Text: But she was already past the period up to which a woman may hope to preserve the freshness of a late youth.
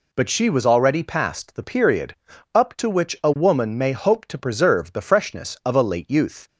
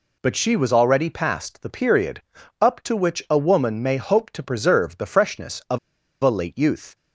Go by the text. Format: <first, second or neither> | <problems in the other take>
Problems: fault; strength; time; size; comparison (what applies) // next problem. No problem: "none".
first | pauses between "period" and "up"; at 2.2 s; 0.38 s long; also in the first // pauses between "of" and "a"; at 5.7 s; 0.43 s long